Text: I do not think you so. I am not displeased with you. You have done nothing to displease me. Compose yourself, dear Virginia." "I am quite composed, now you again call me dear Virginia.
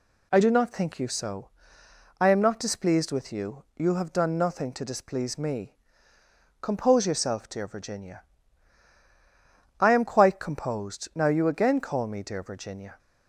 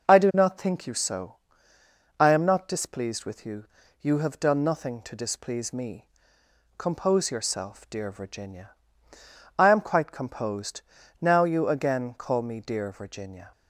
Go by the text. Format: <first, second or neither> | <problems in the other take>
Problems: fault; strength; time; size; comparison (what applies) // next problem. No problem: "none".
neither | none